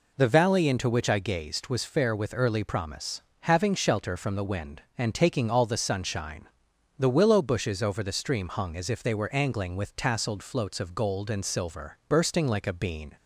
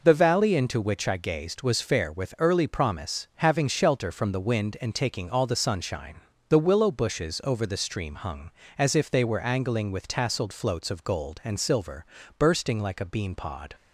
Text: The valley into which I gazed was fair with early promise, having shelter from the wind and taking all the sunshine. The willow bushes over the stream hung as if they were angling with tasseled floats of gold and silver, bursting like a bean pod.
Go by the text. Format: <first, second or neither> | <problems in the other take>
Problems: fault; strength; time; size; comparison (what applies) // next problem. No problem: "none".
second | stops before "pod"; at 13.1 s